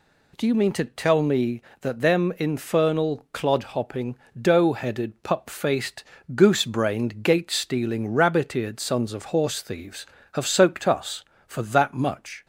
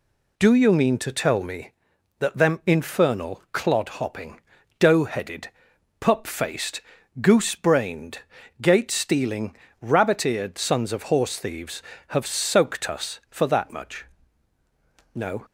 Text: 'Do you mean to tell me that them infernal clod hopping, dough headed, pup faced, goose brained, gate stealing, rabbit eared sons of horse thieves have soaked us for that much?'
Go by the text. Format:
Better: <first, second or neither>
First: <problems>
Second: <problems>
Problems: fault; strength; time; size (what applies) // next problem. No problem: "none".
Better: first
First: none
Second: goes on to say "No"; slight; from 15.1 s on; 0.32 s long